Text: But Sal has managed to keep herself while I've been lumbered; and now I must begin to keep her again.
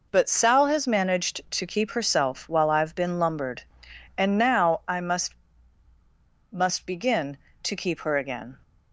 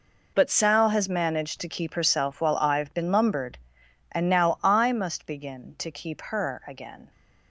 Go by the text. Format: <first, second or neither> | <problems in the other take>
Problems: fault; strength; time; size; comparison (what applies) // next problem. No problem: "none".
second | says "must" twice; at 6.5 s